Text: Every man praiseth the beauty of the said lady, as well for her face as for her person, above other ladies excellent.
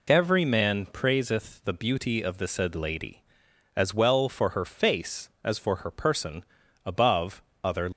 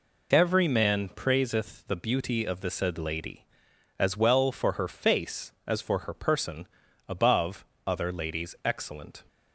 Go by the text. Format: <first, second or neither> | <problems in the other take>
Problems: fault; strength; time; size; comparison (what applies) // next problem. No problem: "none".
second | pauses between "above" and "other"; slight; at 7.4 s; 0.20 s long; slight in the second // stops before "ladies excellent"; at 7.9 s